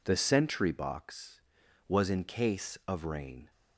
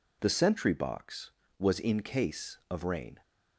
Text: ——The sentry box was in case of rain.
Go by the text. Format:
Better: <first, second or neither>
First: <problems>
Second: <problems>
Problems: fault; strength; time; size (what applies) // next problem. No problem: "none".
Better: neither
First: none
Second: none